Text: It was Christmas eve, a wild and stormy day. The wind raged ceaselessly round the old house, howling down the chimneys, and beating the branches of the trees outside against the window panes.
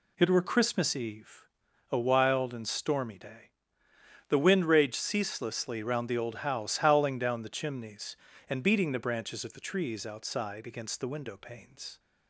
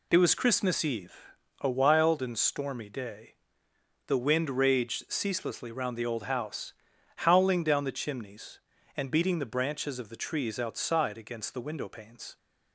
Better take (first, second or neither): second